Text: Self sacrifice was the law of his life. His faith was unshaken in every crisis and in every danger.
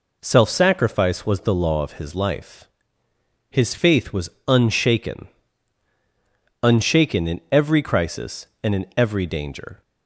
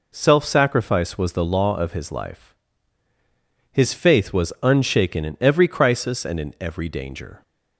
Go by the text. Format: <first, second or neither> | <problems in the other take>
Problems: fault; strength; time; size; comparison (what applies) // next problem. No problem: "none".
second | pauses between "was" and "unshaken"; slight; at 4.2 s; 0.18 s long // says "unshaken" twice; at 6.6 s